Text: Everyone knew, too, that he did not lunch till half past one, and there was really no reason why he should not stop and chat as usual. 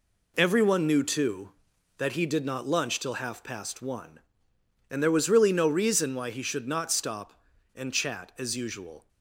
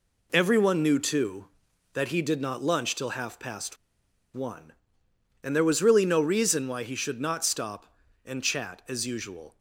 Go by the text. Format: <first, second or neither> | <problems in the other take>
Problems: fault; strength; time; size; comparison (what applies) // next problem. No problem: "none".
first | pauses between "past" and "one"; noticeable; at 3.7 s; 0.57 s long